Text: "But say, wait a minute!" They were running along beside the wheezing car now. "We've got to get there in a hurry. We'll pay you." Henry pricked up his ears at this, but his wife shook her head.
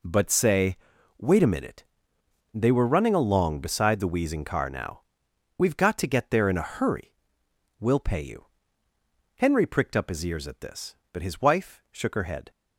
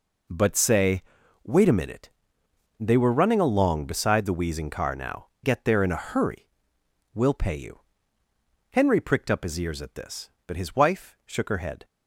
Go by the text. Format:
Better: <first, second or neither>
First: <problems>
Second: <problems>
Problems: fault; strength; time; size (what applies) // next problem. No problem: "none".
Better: first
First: none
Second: skips "We've got to"; at 5.3 s